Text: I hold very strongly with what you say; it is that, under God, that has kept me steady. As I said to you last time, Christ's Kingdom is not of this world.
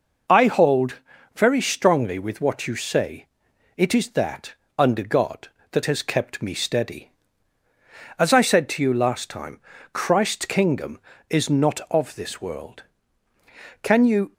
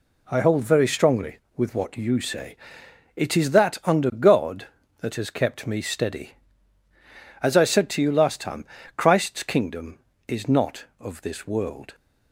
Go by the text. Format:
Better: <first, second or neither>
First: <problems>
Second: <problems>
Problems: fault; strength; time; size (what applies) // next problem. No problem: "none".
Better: second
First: pauses between "hold" and "very"; slight; at 1.0 s; 0.36 s long // goes on to say "Can you"; from 13.8 s on; 0.52 s long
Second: none